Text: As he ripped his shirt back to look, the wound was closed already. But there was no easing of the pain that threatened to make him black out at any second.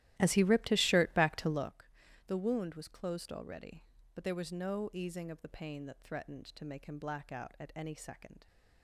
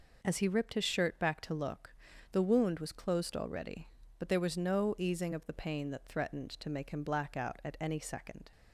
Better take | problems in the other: second | starts louder than the rest; strong; until 1.8 s; 14 dB

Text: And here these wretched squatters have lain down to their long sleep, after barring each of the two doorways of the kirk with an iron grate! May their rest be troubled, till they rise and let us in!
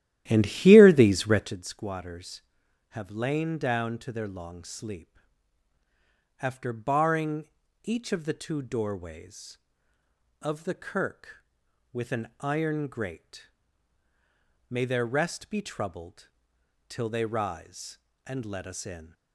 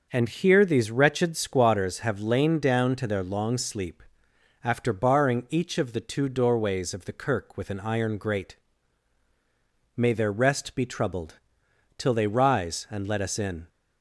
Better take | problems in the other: second | starts louder than the rest; strong; until 1.6 s; 13 dB // pauses between "barring" and "each"; slight; at 7.4 s; 0.36 s long

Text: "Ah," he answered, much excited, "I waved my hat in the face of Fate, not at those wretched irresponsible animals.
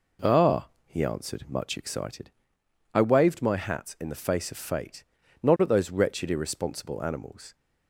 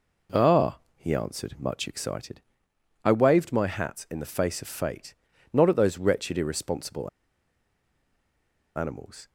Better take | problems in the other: first | pauses between "irresponsible" and "animals"; strong; at 7.0 s; 1.6 s long

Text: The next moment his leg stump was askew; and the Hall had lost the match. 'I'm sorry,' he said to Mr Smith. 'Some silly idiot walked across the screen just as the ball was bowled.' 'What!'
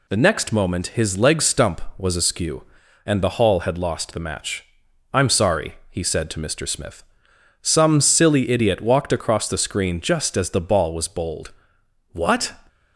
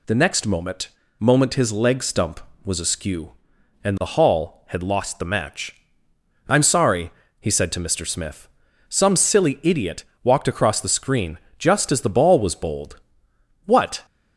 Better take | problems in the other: first | says "moment" twice; at 1.1 s // pauses between "idiot" and "walked"; slight; at 10.0 s; 0.18 s long // pauses between "screen" and "just"; slight; at 11.3 s; 0.20 s long

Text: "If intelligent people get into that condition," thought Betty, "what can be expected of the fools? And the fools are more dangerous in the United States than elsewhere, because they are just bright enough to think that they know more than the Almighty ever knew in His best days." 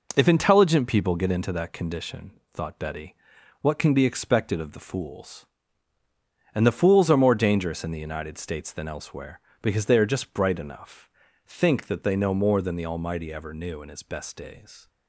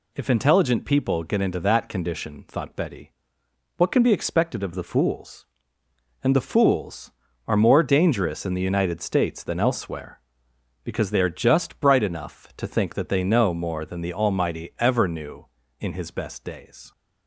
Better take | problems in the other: second | skips "to"; at 11.2 s

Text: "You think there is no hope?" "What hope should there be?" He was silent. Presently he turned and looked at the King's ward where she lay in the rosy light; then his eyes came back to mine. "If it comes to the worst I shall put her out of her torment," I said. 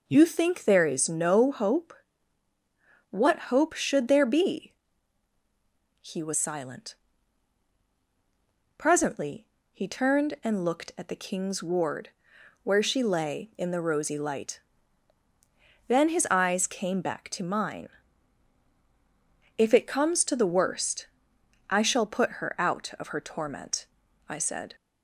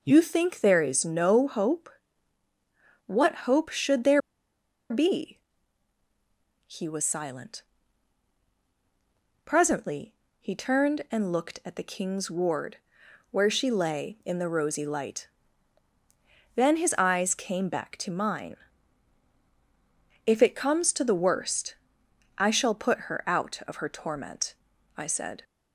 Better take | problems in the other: first | pauses between "there" and "be"; noticeable; at 4.2 s; 0.70 s long // pauses between "Presently" and "he"; slight; at 10.1 s; 0.24 s long; slight in the first // pauses between "ward" and "where"; noticeable; at 12.7 s; 0.54 s long; noticeable in the first // pauses between "worst" and "I"; noticeable; at 21.7 s; 0.62 s long; noticeable in the first

